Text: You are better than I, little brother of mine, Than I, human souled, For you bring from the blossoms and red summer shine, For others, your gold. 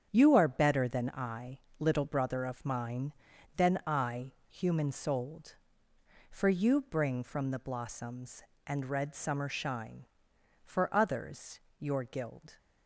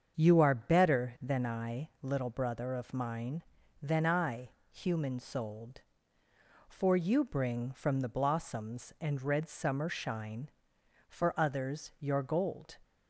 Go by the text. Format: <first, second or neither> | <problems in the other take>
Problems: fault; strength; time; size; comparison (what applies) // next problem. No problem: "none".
second | starts louder than the rest; strong; until 1.1 s; 8 dB; also in the second // says "guild" for "gold"; at 12.0 s